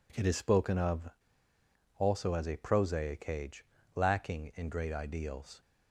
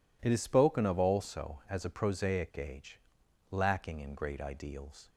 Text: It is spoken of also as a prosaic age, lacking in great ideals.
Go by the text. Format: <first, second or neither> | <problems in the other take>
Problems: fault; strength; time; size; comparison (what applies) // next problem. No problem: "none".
second | pauses between "of" and "also"; noticeable; at 1.0 s; 0.90 s long